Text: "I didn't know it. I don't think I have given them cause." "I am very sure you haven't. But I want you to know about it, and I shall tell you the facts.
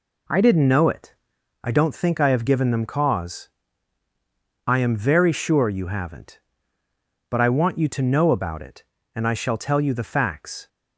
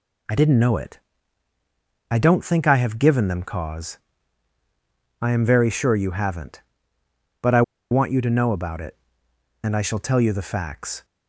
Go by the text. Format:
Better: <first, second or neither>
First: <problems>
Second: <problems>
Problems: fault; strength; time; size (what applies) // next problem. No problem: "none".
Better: first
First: none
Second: pauses between "I" and "want"; slight; at 7.6 s; 0.29 s long